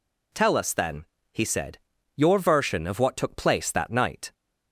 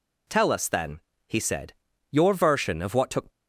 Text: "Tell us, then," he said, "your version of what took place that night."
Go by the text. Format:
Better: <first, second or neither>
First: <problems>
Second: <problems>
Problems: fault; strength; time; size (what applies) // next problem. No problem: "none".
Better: first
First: none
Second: stops before "place that night"; at 3.3 s